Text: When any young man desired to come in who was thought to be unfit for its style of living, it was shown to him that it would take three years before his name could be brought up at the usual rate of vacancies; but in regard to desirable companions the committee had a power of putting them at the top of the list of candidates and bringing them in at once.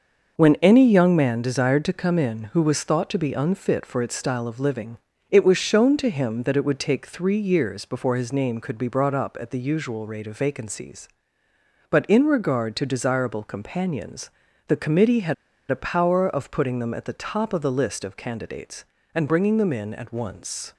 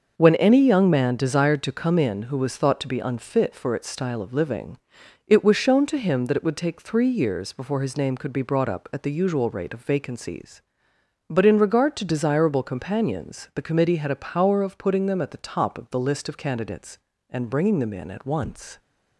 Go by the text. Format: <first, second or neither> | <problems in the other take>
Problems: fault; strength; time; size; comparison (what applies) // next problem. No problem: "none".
second | starts louder than the rest; until 1.4 s; 6 dB // pauses between "companions" and "the"; at 14.2 s; 0.38 s long // pauses between "had" and "a"; slight; at 15.3 s; 0.35 s long